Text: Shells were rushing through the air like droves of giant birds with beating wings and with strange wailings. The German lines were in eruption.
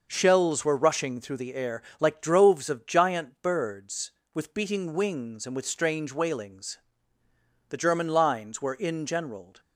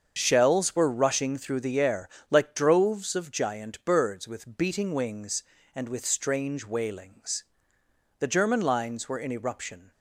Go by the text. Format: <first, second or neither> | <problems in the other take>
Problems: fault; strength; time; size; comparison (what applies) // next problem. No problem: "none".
second | starts louder than the rest; noticeable; until 1.1 s; 6 dB; also in the second // pauses between "air" and "like"; slight; at 1.8 s; 0.18 s long; slight in the second // says "generaled" for "eruption"; at 9.0 s